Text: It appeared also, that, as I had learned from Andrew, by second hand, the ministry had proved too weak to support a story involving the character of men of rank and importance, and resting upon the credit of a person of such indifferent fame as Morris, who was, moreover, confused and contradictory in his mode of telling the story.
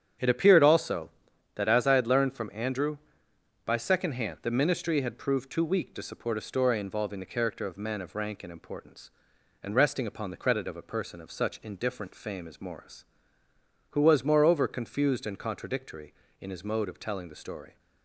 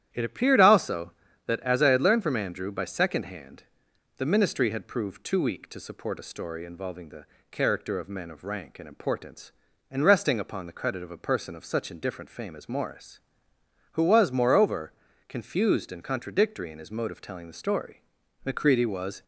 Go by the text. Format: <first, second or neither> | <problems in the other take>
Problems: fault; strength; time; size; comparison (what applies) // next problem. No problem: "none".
first | starts louder than the rest; strong; until 1.1 s; 11 dB; strong in the first // pauses between "the" and "character"; slight; at 7.2 s; 0.26 s long // goes on to say "Macready was"; noticeable; from 18.4 s on; 0.78 s long